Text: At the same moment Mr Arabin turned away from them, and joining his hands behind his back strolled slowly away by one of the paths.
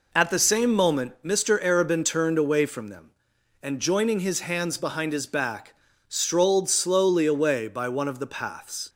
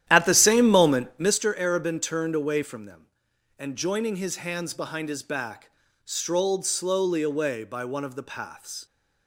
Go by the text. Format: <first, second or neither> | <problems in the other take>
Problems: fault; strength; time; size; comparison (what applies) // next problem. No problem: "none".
first | starts louder than the rest; strong; until 1.4 s; 11.5 dB // pauses between "back" and "strolled"; slight; at 5.7 s; 0.34 s long; slight in the first